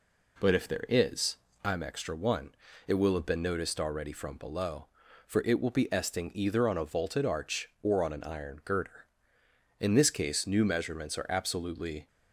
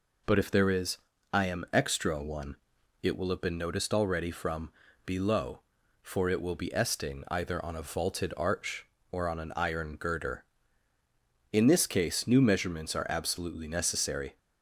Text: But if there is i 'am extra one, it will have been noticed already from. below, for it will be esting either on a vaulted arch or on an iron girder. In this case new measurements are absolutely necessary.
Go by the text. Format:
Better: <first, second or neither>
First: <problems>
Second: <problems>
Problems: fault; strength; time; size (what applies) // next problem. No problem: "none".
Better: second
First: pauses between "is" and "i"; slight; at 1.3 s; 0.28 s long // stops before "necessary"; at 12.0 s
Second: pauses between "is" and "i"; slight; at 0.9 s; 0.36 s long